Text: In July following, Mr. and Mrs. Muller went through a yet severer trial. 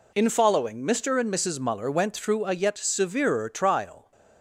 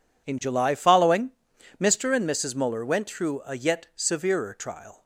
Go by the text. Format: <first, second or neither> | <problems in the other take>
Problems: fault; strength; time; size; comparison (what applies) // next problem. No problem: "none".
second | skips "July"; at 0.2 s